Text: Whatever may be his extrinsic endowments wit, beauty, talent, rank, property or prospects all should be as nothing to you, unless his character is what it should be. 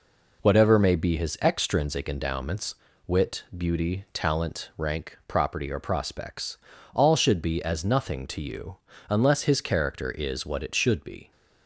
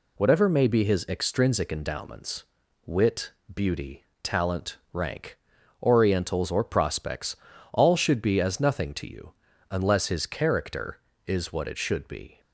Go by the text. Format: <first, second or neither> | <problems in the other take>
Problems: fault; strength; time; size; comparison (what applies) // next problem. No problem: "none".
first | pauses between "endowments" and "wit"; at 2.4 s; 0.42 s long; slight in the first // says "orientals" for "property"; at 5.8 s // pauses between "prospects" and "all"; at 7.3 s; 0.38 s long; also in the first